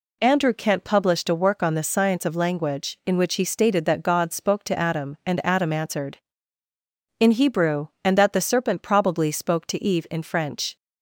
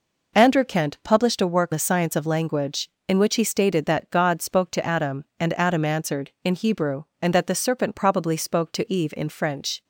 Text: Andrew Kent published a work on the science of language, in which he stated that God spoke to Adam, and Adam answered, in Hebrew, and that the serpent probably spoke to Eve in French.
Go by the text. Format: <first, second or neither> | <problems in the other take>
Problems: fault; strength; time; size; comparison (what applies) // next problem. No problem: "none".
first | skips "on"; at 1.7 s